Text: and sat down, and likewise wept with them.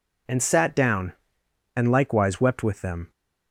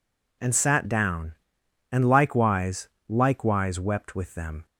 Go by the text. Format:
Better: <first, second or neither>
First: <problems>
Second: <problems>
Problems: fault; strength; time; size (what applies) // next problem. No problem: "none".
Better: first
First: none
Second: says "likewise" twice; at 3.0 s